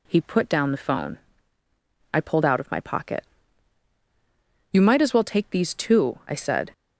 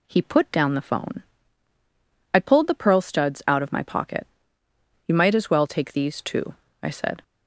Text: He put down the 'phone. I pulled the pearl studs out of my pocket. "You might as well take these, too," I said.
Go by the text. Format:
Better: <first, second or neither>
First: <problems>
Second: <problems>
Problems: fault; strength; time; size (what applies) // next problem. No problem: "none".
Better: second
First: skips "the pearl studs"; at 2.4 s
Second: none